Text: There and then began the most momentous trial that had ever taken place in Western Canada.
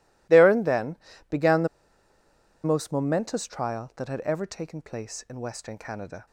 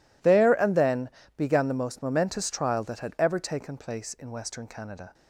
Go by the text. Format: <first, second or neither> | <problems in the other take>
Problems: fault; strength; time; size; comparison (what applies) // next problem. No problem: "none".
second | pauses between "then" and "began"; slight; at 0.9 s; 0.34 s long; slight in the second // pauses between "the" and "most"; noticeable; at 1.6 s; 0.97 s long